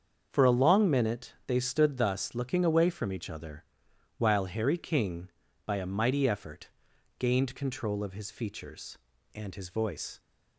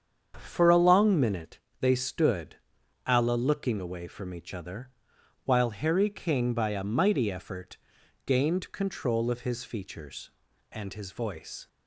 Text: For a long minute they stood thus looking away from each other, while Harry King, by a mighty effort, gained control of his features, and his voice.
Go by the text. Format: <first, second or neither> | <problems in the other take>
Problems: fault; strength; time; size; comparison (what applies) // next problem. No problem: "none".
first | starts louder than the rest; strong; until 1.4 s; 7.5 dB; also in the first // pauses between "minute" and "they"; slight; at 1.5 s; 0.20 s long // says "alla" for "thus"; at 3.0 s